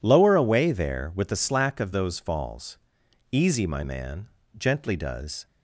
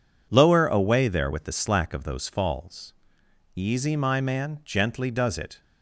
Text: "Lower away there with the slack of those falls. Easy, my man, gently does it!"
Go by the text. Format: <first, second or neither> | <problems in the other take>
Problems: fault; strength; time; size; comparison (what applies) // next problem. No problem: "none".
second | stops before "it"; at 5.4 s